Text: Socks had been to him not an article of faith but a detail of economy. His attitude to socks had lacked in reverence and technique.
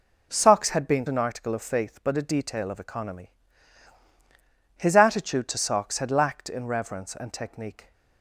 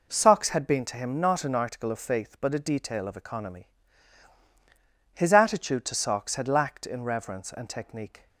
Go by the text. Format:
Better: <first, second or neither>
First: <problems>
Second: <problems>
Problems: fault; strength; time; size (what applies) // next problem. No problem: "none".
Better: second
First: skips "to him not"; at 1.0 s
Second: none